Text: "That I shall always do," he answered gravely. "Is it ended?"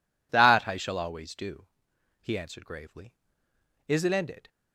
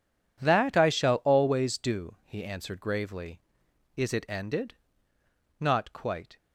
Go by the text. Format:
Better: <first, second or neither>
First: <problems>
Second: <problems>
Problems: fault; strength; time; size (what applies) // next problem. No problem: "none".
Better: first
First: none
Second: goes on to say "Not quite"; noticeable; from 5.5 s on; 0.78 s long